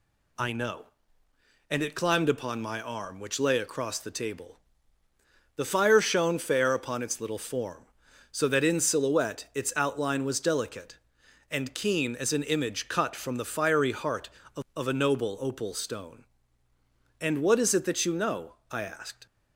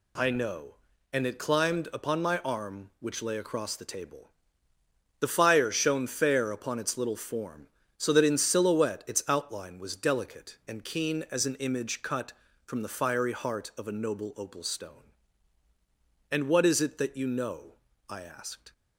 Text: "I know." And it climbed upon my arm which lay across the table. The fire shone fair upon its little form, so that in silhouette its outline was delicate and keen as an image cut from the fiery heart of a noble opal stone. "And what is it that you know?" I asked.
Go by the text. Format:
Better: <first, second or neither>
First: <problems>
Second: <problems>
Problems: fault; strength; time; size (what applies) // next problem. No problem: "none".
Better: second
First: says "of" twice; at 14.7 s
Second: none